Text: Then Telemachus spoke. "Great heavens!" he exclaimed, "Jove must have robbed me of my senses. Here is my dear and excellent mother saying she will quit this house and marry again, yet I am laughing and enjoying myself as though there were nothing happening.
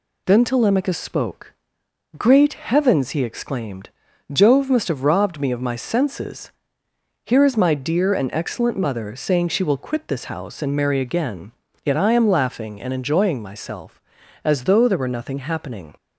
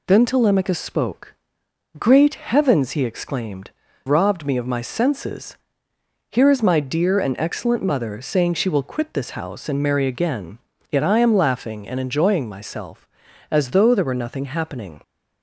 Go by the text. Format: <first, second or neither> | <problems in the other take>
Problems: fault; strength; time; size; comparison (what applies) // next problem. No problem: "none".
first | skips "Jove must have"; at 3.8 s